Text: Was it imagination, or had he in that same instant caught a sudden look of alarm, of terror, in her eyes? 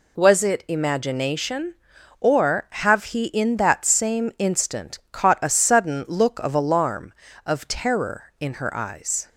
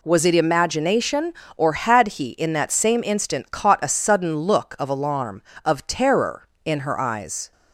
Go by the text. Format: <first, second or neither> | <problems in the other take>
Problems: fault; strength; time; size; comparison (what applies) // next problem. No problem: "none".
second | says "have" for "had"; at 2.6 s